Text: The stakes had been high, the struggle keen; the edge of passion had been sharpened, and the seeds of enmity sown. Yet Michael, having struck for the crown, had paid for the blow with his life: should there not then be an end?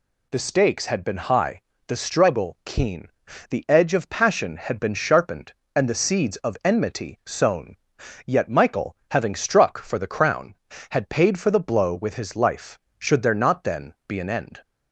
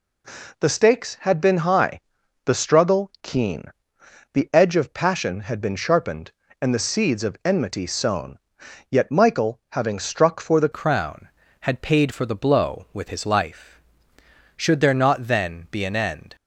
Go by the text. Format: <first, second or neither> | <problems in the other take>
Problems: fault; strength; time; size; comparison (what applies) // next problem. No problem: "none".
first | changes voice at "crown"; from 10.7 s on; 5.6 s long